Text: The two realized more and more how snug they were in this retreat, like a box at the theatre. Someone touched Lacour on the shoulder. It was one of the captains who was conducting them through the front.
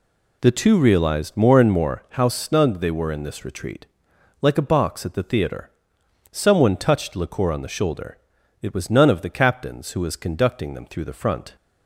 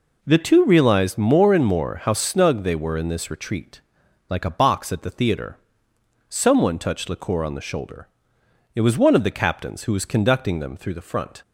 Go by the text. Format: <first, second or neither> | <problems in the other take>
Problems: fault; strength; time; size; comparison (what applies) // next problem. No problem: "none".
second | says "none" for "one"; at 8.8 s